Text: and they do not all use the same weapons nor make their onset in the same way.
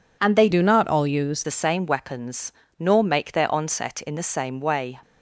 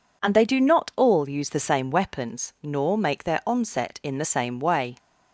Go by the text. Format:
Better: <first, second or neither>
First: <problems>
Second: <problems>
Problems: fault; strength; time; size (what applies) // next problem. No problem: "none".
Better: second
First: changes voice from "do" to "use"; from 0.5 to 1.4 s; 0.9 s long // pauses between "weapons" and "nor"; slight; at 2.5 s; 0.26 s long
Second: none